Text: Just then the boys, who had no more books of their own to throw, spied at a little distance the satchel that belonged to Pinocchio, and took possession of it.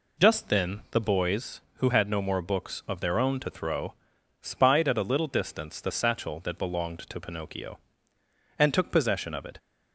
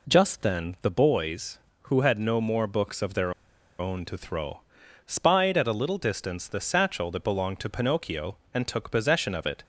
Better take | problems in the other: first | pauses between "their" and "own"; noticeable; at 3.3 s; 0.46 s long

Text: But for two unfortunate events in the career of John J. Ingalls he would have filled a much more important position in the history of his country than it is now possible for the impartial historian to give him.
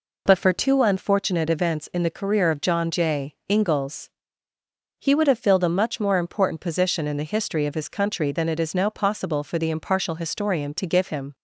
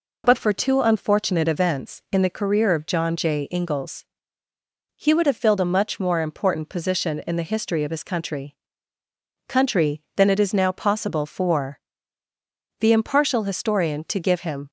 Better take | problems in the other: first | pauses between "Ingalls" and "he"; noticeable; at 4.0 s; 0.94 s long; noticeable in the first // says "country" twice; at 9.4 s // pauses between "for" and "the"; at 11.7 s; 1.0 s long

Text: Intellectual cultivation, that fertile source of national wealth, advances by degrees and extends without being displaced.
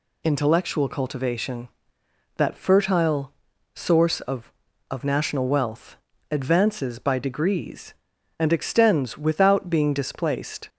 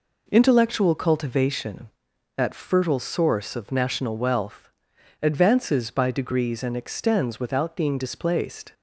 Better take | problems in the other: second | pauses between "fertile" and "source"; at 3.3 s; 0.42 s long // says "of" twice; at 4.8 s

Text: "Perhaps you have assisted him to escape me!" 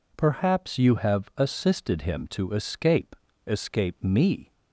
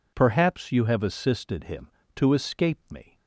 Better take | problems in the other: second | says "escape" twice; at 3.4 s

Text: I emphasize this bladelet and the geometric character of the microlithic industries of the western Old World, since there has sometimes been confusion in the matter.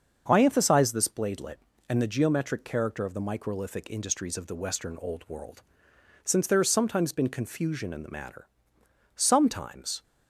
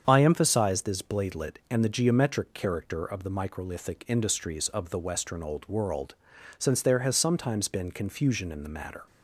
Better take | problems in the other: second | starts louder than the rest; until 1.2 s; 6.5 dB; strong in the second // goes on to say "Sometimes"; noticeable; from 9.1 s on; 0.88 s long

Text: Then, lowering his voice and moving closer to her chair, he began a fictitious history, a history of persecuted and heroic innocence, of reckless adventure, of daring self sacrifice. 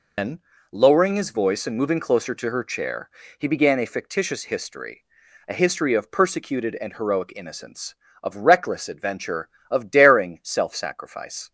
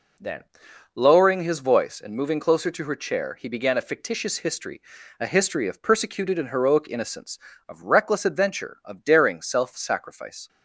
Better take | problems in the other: second | loses the start of "Then"; at 0.1 s; 130 ms

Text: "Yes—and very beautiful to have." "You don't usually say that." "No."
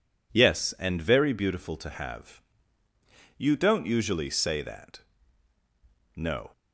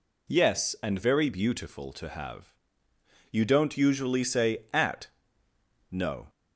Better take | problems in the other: first | says "at" for "that"; at 4.7 s

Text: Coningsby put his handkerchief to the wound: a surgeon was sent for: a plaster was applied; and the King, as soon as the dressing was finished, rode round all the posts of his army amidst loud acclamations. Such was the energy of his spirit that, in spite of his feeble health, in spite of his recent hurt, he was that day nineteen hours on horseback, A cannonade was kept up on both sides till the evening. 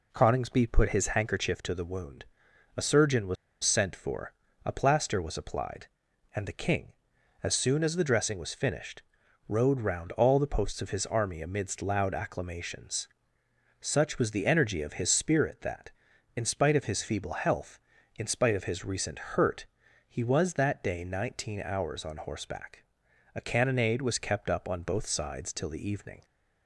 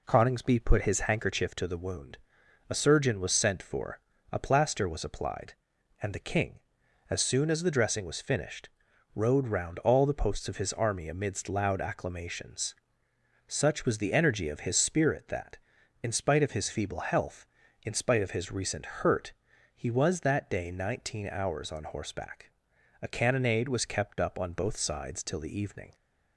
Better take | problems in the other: second | pauses between "was" and "sent"; slight; at 3.3 s; 0.29 s long

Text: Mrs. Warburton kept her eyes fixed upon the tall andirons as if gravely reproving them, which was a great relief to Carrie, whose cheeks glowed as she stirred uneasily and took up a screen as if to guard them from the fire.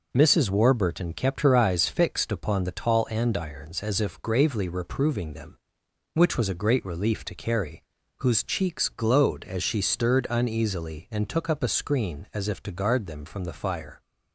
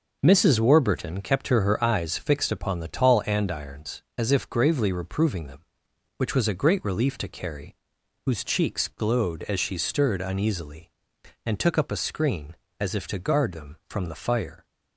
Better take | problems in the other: first | says "her" twice; at 1.6 s

